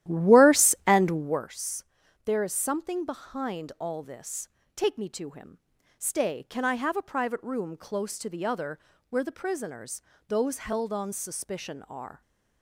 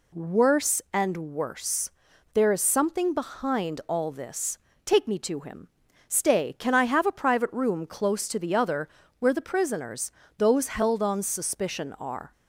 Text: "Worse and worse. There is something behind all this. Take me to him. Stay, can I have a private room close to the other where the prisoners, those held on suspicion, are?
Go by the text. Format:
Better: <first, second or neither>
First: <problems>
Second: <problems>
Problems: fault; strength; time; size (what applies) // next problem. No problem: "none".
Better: second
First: starts louder than the rest; strong; until 1.5 s; 12.5 dB // pauses between "other" and "where"; slight; at 8.7 s; 0.32 s long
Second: pauses between "other" and "where"; slight; at 8.8 s; 0.32 s long